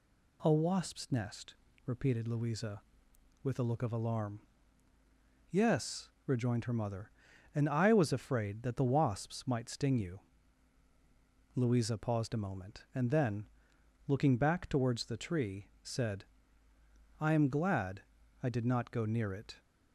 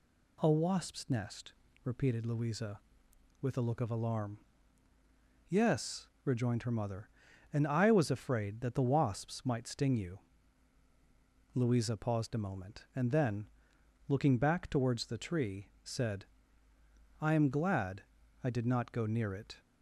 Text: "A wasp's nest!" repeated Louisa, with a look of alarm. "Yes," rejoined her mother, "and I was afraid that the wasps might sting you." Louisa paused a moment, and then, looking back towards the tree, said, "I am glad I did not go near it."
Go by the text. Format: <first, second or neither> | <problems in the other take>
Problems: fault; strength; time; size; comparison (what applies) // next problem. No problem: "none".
neither | pauses between "glad" and "I"; the same in both